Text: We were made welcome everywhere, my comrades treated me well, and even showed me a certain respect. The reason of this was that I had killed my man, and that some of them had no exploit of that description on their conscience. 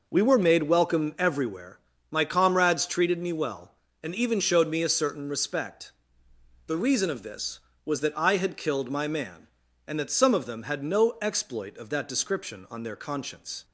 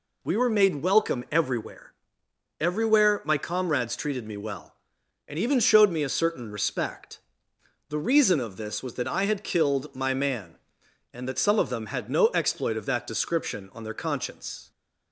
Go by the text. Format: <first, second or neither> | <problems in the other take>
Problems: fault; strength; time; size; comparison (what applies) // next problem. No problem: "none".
first | says "everywhere" twice; at 2.5 s